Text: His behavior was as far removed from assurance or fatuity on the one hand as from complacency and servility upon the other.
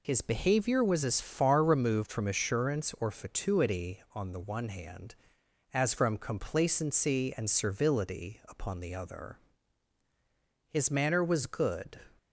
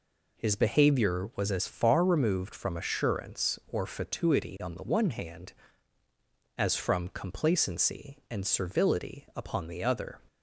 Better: second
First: goes on to say "His manner was good"; noticeable; from 10.7 s on; 1.2 s long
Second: none

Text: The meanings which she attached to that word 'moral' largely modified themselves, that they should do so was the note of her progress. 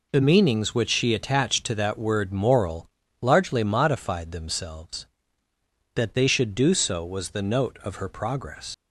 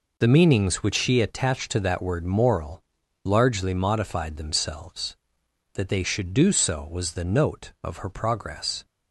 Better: second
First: pauses between "moral" and "largely"; slight; at 2.8 s; 0.32 s long // leaves "progress" unfinished; at 8.7 s; 70 ms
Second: pauses between "moral" and "largely"; at 2.8 s; 0.40 s long

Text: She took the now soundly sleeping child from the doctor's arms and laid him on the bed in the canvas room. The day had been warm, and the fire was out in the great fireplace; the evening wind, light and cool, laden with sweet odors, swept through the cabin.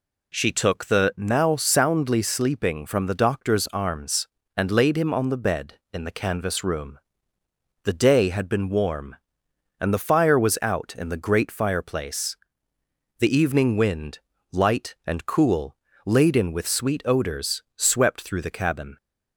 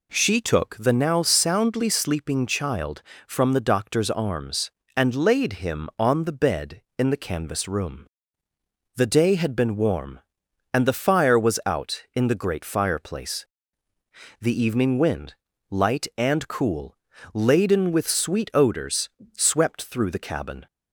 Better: second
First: skips "child"; at 2.8 s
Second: none

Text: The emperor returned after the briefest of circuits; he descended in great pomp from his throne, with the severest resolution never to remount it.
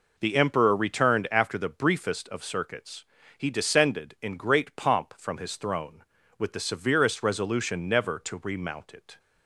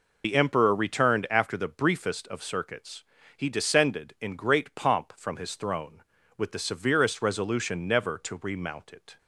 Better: first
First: none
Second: loses the start of "The"; at 0.2 s; 70 ms

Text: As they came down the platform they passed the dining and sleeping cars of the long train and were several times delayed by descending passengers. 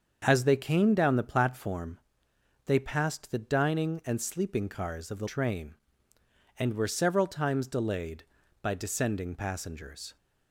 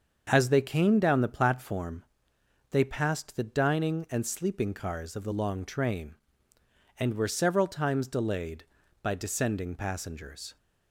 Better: second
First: starts louder than the rest; until 1.2 s; 7 dB // pauses between "platform" and "they"; noticeable; at 1.9 s; 0.66 s long // skips "long"; at 5.2 s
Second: starts louder than the rest; until 1.3 s; 7 dB // pauses between "platform" and "they"; noticeable; at 2.0 s; 0.66 s long

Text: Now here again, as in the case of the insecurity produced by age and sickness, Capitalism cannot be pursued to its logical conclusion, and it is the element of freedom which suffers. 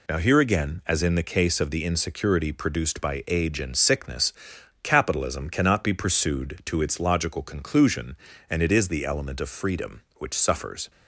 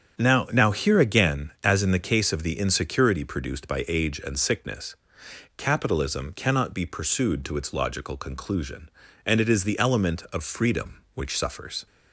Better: first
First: none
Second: starts louder than the rest; strong; until 1.2 s; 8 dB // says "Now" twice; at 0.4 s

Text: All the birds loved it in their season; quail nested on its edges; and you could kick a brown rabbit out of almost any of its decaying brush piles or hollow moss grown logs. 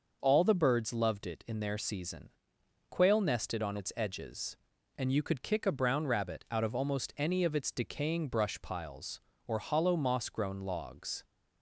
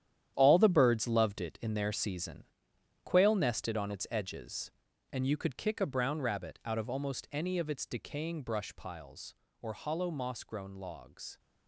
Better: first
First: none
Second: gets quieter; strong; throughout; 11.5 dB

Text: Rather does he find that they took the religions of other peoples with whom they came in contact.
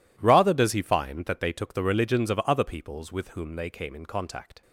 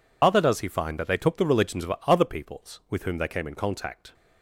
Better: first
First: none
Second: loses the start of "Rather"; at 0.2 s; 155 ms

